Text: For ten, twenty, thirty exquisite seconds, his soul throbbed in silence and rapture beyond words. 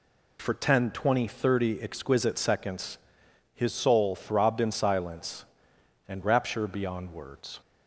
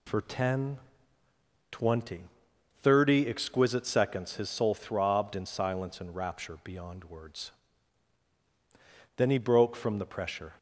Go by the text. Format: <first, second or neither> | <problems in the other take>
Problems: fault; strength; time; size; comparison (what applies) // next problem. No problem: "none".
first | goes on to say "Then he broke from the pressure"; from 9.1 s on; 1.3 s long